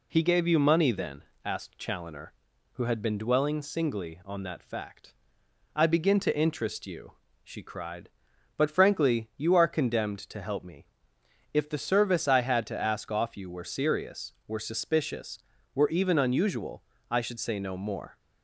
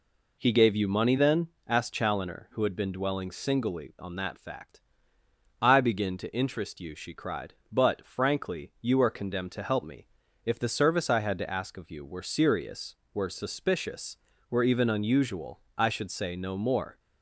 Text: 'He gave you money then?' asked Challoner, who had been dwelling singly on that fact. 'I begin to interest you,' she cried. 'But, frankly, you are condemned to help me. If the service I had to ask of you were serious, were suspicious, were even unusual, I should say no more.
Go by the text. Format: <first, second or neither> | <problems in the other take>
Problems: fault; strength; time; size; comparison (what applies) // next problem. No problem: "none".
second | says "off" for "of"; at 13.0 s